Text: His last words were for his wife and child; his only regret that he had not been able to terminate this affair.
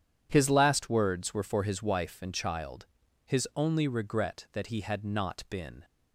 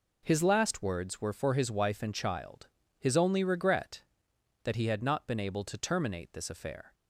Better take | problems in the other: second | stops before "able to terminate this affair"; at 5.8 s

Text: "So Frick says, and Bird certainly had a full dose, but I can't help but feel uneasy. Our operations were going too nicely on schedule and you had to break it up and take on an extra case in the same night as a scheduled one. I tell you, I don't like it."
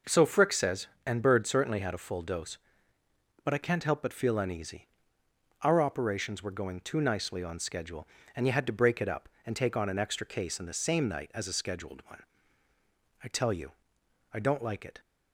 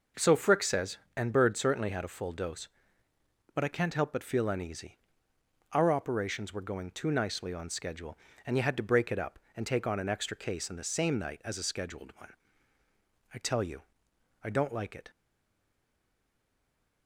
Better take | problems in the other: first | stays silent after the last word; noticeable; from 15.1 s on; 1.9 s long

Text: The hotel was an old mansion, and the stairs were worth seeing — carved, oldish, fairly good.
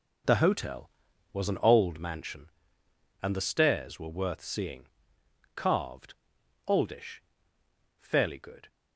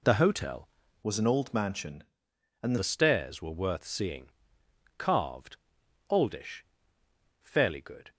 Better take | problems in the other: first | changes voice from "was" to "and"; from 1.0 to 2.7 s; 1.7 s long

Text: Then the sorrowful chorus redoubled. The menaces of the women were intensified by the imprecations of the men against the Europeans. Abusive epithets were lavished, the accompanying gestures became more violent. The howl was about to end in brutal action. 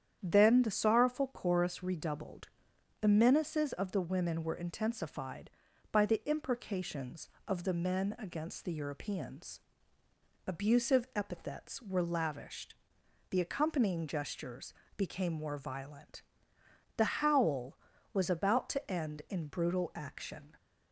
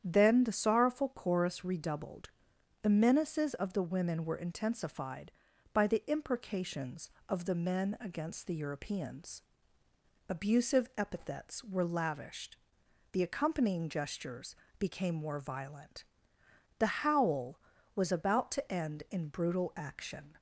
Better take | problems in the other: neither | starts louder than the rest; strong; the same in both // pauses between "gestures" and "became"; slight; the same in both

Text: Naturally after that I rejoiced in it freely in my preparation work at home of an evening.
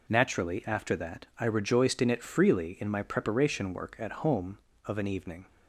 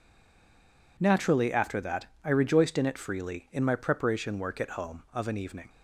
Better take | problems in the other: first | stays silent before the first word; until 0.9 s; 0.9 s long // pauses between "that" and "I"; slight; at 2.0 s; 0.18 s long

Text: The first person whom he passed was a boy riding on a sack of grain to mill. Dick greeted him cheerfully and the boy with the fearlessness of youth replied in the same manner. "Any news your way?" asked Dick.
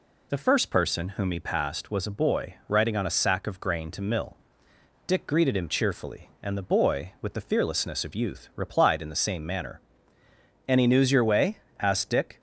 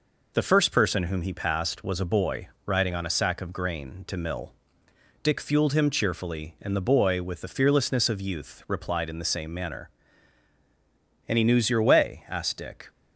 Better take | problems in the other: first | pauses between "boy" and "riding"; slight; at 2.4 s; 0.16 s long // says "fueled" for "greeted"; at 5.3 s

